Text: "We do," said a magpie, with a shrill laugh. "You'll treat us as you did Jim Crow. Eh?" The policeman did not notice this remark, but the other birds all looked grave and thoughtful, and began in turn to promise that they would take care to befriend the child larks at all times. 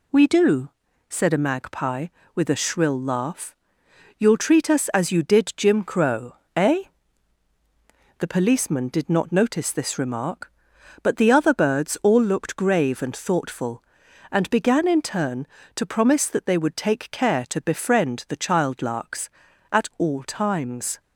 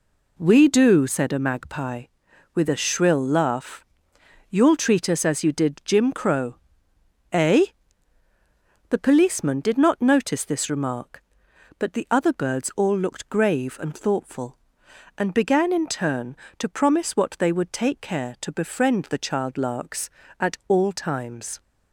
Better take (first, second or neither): first